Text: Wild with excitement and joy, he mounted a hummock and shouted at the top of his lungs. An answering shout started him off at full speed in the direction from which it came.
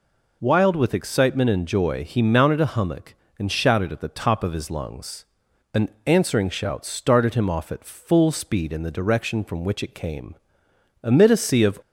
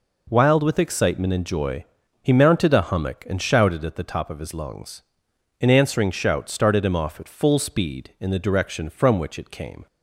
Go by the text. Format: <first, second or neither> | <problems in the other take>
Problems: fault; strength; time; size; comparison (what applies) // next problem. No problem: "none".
second | pauses between "An" and "answering"; slight; at 5.8 s; 0.18 s long // goes on to say "Amid a sea of"; noticeable; from 11.0 s on; 0.76 s long